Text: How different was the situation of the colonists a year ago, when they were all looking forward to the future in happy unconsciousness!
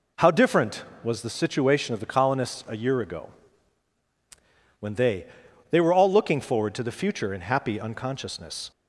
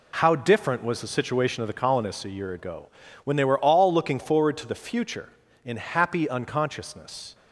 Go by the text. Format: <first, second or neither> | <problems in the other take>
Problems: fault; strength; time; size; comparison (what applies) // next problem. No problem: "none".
second | says "they" twice; at 5.7 s